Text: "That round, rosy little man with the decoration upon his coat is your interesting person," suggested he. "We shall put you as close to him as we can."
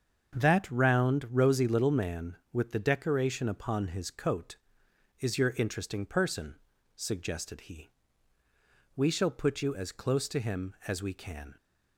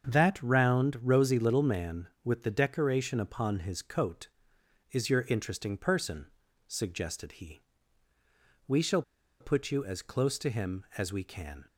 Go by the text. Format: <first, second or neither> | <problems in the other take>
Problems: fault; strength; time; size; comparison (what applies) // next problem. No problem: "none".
first | starts louder than the rest; strong; until 1.1 s; 7 dB; strong in the first // pauses between "shall" and "put"; at 9.0 s; 0.39 s long